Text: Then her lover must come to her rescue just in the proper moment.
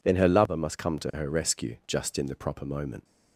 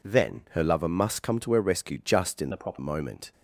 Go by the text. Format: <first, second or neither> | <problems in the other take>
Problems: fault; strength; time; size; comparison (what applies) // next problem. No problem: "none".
first | changes voice from "the" to "proper"; from 2.5 to 2.7 s; 0.2 s long